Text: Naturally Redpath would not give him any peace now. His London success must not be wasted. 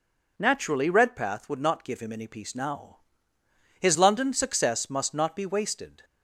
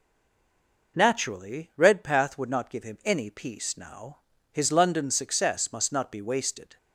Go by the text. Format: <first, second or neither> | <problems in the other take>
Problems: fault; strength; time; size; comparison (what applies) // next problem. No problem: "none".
first | stays silent before the first word; slight; until 0.9 s; 0.9 s long